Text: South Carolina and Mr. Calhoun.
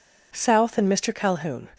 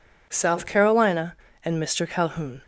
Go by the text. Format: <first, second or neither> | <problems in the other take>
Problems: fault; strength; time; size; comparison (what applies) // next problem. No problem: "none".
second | skips "Carolina"; at 0.7 s